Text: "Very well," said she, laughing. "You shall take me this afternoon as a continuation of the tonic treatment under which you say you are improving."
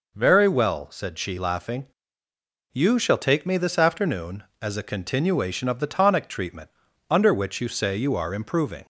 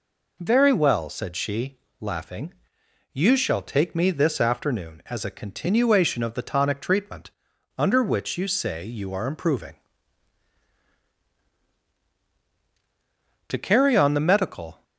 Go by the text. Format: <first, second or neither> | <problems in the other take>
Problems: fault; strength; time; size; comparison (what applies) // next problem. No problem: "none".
first | pauses between "treatment" and "under"; noticeable; at 7.2 s; 0.48 s long; also in the first // goes on to say "To carry on the medical"; from 13.4 s on; 1.3 s long